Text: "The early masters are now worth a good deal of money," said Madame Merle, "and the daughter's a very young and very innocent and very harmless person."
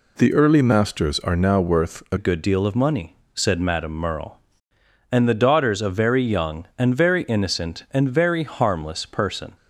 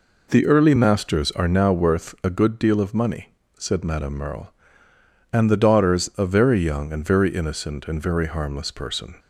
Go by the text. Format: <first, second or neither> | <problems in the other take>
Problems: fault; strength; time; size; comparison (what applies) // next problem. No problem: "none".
second | changes voice at "good"; from 2.1 s on; 7.4 s long